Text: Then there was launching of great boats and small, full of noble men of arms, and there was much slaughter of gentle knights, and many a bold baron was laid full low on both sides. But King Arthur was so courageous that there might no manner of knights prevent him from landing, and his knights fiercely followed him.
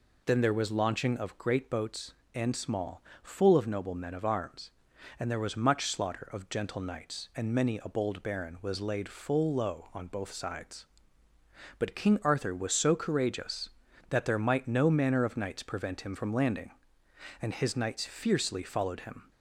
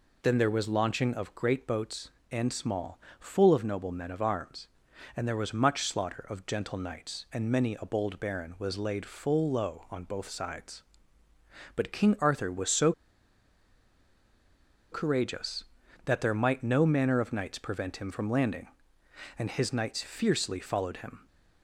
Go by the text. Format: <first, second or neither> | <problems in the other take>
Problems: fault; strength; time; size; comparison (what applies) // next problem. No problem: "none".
first | pauses between "so" and "courageous"; strong; at 12.9 s; 2.0 s long